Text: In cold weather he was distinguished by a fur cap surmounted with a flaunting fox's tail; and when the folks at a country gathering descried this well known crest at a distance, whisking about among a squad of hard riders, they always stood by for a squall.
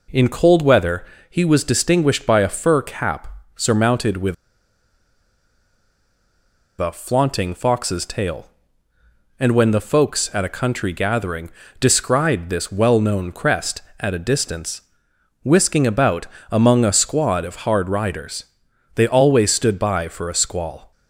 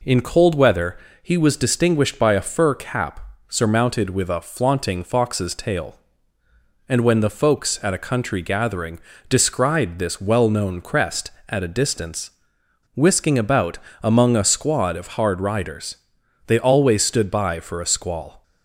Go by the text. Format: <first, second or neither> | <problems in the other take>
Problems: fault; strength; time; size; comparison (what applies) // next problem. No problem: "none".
second | pauses between "weather" and "he"; slight; at 1.0 s; 0.24 s long; slight in the second // pauses between "cap" and "surmounted"; slight; at 3.2 s; 0.28 s long; slight in the second // pauses between "with" and "a"; strong; at 4.3 s; 2.4 s long // pauses between "gathering" and "descried"; slight; at 11.4 s; 0.30 s long; slight in the second // pauses between "about" and "among"; slight; at 16.2 s; 0.24 s long; slight in the second